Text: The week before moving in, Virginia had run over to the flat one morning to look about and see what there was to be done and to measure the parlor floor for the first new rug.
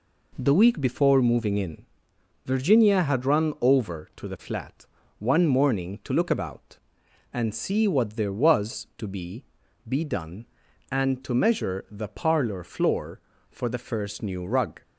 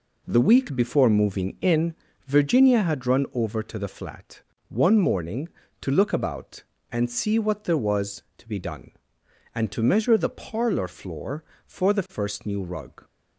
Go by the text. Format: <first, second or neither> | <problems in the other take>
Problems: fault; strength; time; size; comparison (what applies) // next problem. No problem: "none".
second | pauses between "flat" and "one"; slight; at 4.8 s; 0.32 s long; slight in the second // says "be" twice; at 9.8 s